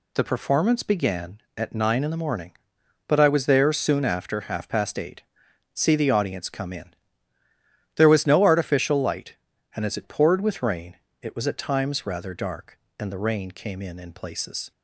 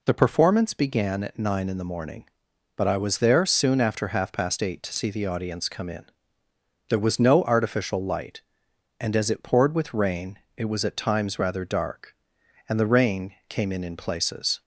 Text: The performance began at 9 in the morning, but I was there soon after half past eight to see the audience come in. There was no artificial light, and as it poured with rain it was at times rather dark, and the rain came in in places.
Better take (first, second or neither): second